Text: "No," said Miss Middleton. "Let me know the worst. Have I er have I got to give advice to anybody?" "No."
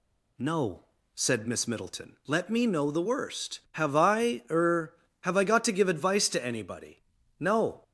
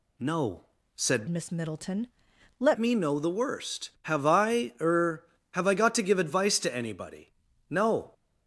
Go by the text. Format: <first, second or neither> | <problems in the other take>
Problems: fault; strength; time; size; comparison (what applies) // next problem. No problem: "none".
first | changes voice from "Miss" to "Let"; from 1.2 to 2.7 s; 1.5 s long